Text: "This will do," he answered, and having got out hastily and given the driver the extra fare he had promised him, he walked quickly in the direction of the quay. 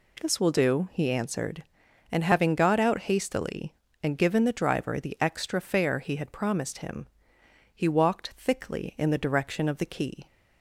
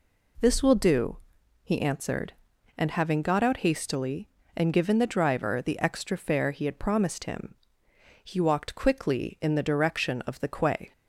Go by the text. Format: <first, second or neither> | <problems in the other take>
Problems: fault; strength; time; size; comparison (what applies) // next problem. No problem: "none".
second | says "thickly" for "quickly"; at 8.3 s